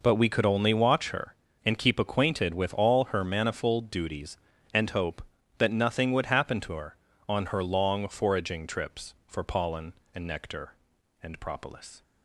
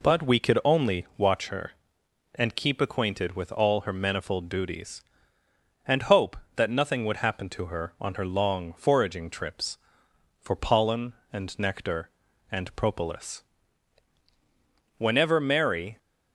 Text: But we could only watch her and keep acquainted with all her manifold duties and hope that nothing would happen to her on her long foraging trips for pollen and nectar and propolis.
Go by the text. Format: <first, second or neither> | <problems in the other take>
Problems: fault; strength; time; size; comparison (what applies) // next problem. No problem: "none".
first | goes on to say "Whenever Mary"; noticeable; from 14.9 s on; 1.0 s long